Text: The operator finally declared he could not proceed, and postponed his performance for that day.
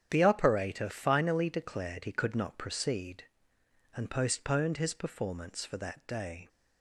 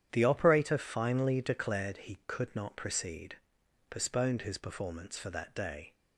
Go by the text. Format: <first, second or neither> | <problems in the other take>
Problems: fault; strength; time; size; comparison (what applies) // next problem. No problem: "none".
first | starts louder than the rest; strong; until 1.1 s; 9.5 dB; strong in the first // skips "and"; at 3.6 s